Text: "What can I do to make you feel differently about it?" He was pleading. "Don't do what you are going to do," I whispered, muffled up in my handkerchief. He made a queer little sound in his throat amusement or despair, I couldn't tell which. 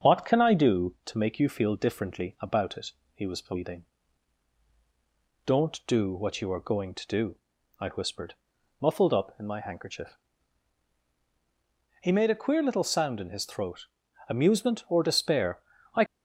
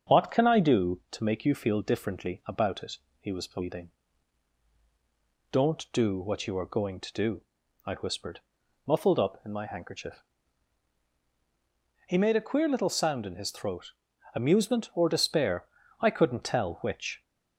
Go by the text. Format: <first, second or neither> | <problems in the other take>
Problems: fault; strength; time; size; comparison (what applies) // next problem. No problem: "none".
second | starts louder than the rest; strong; until 1.0 s; 7 dB; also in the second // pauses between "throat" and "amusement"; at 13.8 s; 0.42 s long; also in the second // stops before "couldn't tell which"; at 16.0 s